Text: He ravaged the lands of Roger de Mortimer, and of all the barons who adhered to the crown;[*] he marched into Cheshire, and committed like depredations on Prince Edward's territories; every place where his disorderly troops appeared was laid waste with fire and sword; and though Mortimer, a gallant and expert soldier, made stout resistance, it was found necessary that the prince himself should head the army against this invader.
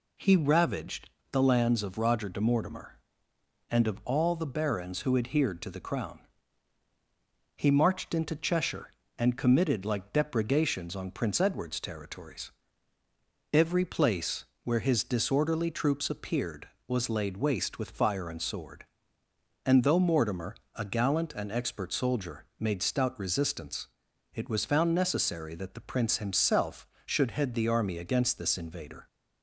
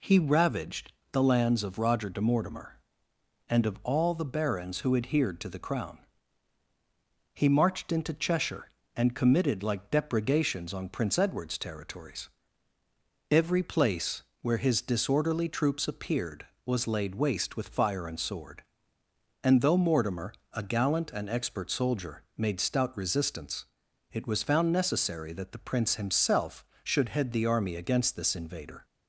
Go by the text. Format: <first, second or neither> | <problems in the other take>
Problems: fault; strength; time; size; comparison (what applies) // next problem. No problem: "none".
neither | pauses between "ravaged" and "the"; slight; the same in both // pauses between "place" and "where"; slight; the same in both